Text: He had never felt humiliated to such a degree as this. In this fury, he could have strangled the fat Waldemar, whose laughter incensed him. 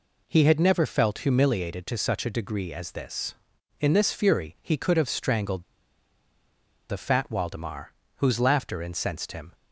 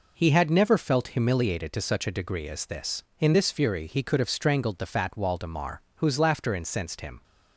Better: second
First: pauses between "strangled" and "the"; strong; at 5.6 s; 1.2 s long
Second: none

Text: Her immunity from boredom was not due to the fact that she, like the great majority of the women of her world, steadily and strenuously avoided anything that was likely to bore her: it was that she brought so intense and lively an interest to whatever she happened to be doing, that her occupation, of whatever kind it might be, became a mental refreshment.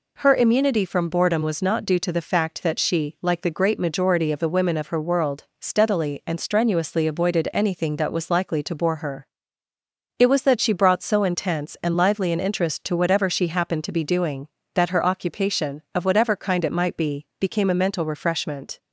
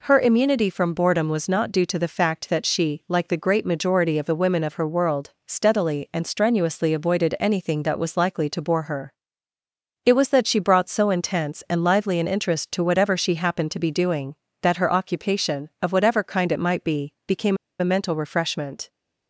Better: first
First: none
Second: pauses between "became" and "a"; slight; at 17.5 s; 0.24 s long

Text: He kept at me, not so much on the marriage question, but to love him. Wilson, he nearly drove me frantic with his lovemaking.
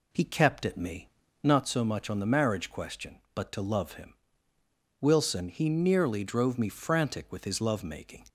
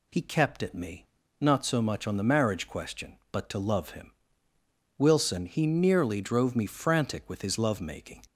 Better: second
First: starts louder than the rest; slight; until 1.6 s; 2.5 dB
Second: none

